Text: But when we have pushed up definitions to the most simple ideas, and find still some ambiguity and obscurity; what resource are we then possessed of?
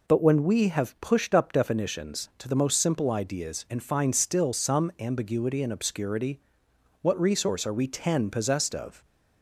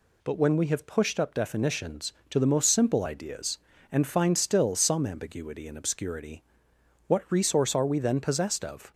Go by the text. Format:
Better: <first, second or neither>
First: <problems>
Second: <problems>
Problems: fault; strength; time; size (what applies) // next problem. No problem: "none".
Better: second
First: says "ten" for "then"; at 7.8 s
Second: none